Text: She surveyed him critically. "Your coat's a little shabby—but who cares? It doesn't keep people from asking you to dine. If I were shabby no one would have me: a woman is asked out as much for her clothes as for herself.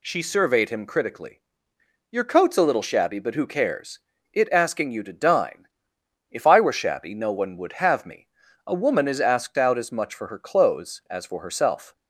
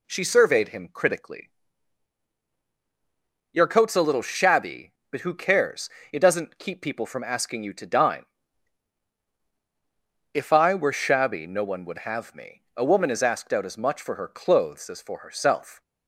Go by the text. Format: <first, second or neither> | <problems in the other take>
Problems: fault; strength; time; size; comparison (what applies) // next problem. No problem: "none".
second | skips "doesn't keep people from"; at 4.5 s